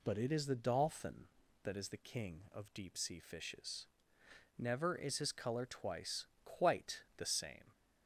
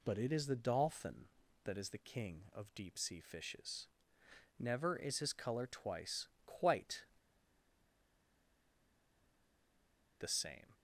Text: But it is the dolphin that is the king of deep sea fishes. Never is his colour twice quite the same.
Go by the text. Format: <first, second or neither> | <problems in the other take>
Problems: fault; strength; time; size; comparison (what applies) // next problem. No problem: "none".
first | pauses between "twice" and "quite"; slight; at 6.2 s; 0.20 s long; slight in the first // pauses between "quite" and "the"; strong; at 7.0 s; 3.1 s long